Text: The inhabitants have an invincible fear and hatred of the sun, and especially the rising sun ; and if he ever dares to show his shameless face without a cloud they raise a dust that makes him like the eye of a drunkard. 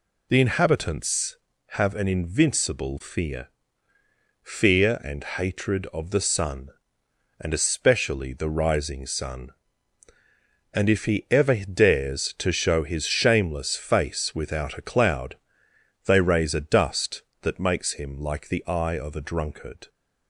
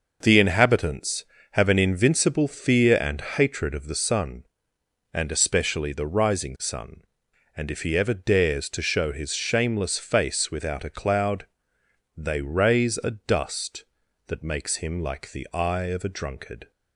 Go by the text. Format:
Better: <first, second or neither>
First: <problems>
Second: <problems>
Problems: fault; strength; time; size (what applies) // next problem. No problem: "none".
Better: second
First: says "fear" twice; at 4.4 s // pauses between "cloud" and "they"; noticeable; at 15.3 s; 0.68 s long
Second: pauses between "cloud" and "they"; noticeable; at 11.4 s; 0.72 s long